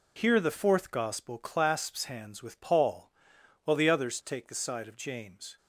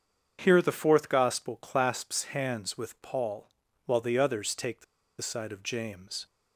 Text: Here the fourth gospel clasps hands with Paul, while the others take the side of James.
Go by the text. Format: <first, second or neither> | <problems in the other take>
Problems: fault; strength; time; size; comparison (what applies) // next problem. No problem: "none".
first | starts louder than the rest; until 1.4 s; 7 dB // pauses between "the" and "side"; at 4.8 s; 0.36 s long